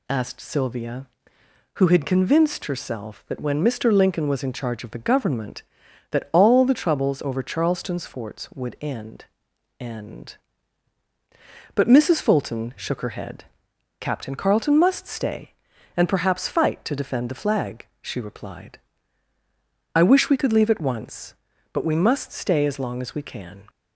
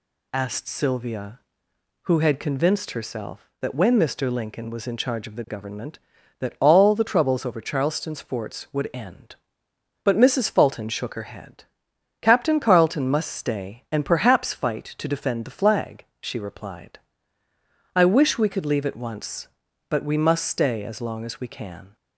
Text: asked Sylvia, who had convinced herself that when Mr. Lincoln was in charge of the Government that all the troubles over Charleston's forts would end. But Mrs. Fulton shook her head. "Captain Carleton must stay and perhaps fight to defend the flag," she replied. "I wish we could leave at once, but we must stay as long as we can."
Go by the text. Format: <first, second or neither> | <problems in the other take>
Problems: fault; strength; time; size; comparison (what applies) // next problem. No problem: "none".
second | says "end" twice; at 9.8 s